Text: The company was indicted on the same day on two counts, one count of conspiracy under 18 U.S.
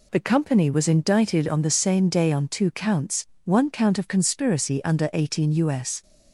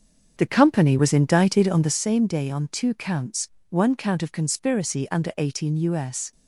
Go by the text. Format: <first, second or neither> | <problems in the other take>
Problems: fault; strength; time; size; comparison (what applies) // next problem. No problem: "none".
first | starts louder than the rest; strong; until 2.0 s; 7 dB